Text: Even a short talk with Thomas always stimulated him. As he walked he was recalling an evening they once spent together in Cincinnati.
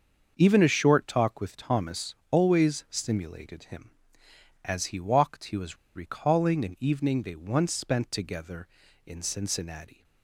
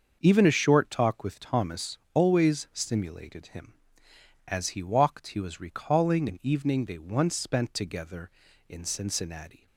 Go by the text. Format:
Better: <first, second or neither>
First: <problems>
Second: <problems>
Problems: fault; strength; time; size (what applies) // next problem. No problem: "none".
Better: second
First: starts louder than the rest; until 1.3 s; 6.5 dB // pauses between "Thomas" and "always"; slight; at 2.1 s; 0.16 s long // pauses between "was" and "recalling"; slight; at 5.7 s; 0.18 s long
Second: starts louder than the rest; until 1.2 s; 6.5 dB // pauses between "Thomas" and "always"; slight; at 1.9 s; 0.16 s long